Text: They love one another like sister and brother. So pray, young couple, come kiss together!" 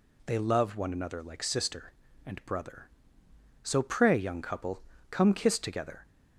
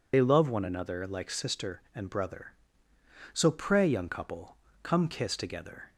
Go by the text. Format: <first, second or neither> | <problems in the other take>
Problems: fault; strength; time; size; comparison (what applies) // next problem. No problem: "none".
first | loses the start of "They"; at 0.1 s; 45 ms